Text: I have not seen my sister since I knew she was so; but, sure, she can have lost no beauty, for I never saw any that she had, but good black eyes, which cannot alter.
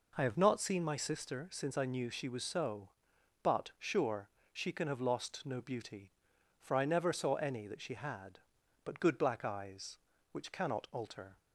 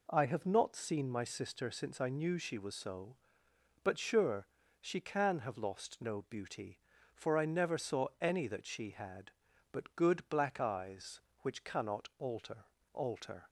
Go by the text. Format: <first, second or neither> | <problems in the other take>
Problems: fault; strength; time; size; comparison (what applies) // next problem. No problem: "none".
first | says "alter" twice; at 12.9 s